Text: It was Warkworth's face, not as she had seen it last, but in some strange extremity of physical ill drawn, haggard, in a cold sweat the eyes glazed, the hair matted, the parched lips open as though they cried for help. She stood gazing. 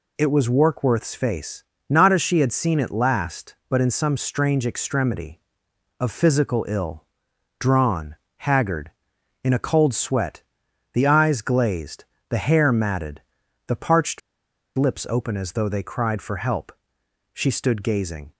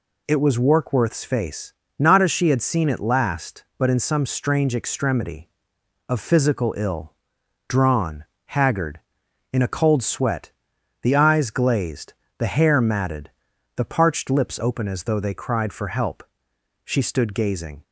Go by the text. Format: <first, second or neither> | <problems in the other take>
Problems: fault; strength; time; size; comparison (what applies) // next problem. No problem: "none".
second | pauses between "ill" and "drawn"; noticeable; at 7.0 s; 0.54 s long; noticeable in the second // pauses between "sweat" and "the"; noticeable; at 10.4 s; 0.52 s long; noticeable in the second // pauses between "parched" and "lips"; noticeable; at 14.1 s; 0.57 s long